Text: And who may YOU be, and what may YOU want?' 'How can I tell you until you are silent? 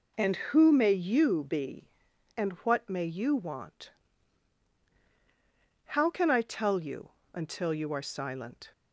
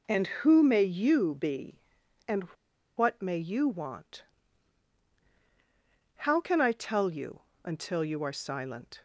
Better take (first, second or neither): first